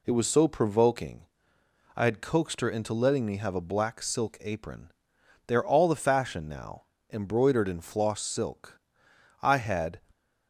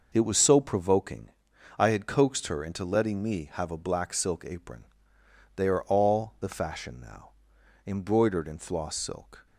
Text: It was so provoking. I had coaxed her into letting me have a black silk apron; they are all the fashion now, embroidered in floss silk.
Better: second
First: goes on to say "I had"; from 9.4 s on; 0.58 s long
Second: none

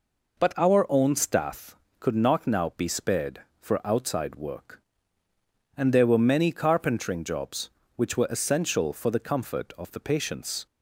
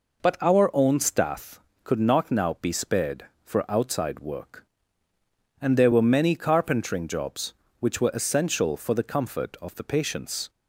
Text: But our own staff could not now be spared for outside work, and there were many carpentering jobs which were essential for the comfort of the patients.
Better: neither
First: none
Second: none

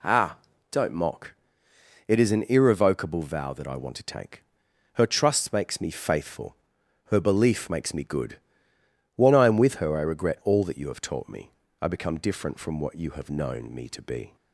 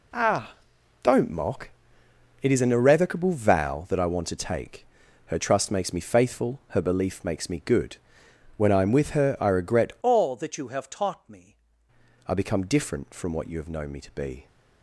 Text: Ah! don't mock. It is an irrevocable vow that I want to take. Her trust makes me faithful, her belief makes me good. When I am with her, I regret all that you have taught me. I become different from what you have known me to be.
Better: first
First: none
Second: changes voice from "all" to "me"; from 10.0 to 11.5 s; 1.5 s long

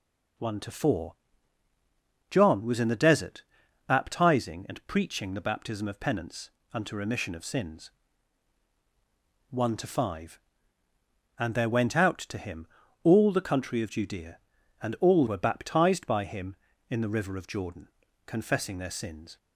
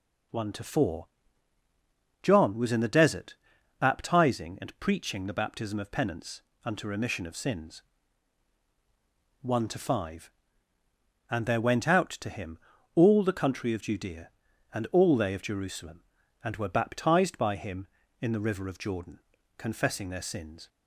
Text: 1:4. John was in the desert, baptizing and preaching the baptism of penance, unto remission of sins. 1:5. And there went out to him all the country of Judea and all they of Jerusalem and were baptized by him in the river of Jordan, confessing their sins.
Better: second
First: pauses between "him" and "all"; at 12.6 s; 0.38 s long // skips "they of Jerusalem and"; at 15.2 s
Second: pauses between "him" and "all"; at 12.5 s; 0.38 s long

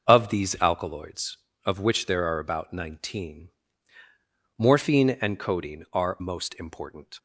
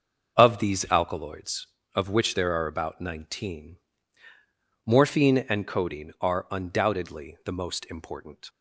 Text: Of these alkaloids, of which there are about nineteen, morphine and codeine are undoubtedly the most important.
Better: second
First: starts louder than the rest; noticeable; until 1.1 s; 6 dB // skips "undoubtedly the"; at 6.2 s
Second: starts louder than the rest; until 1.4 s; 6.5 dB

